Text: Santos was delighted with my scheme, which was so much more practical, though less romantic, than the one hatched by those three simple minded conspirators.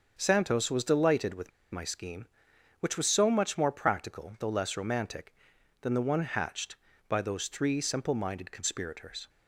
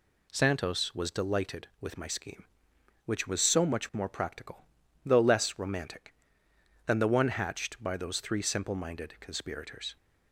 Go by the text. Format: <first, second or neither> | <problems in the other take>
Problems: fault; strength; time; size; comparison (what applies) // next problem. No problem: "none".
second | starts louder than the rest; until 1.2 s; 7 dB // pauses between "with" and "my"; slight; at 1.5 s; 0.22 s long